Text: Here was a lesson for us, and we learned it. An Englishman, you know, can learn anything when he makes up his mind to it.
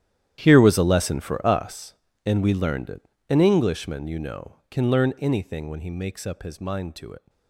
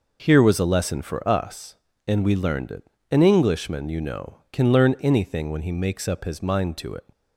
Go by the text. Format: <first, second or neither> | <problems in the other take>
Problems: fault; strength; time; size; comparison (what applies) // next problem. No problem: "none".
second | gets quieter; strong; throughout; 18 dB